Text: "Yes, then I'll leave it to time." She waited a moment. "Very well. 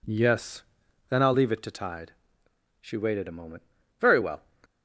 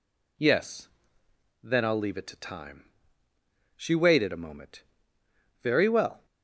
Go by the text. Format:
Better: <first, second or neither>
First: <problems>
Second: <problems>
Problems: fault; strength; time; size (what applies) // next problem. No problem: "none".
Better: second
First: says "tide" for "time"; at 1.7 s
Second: none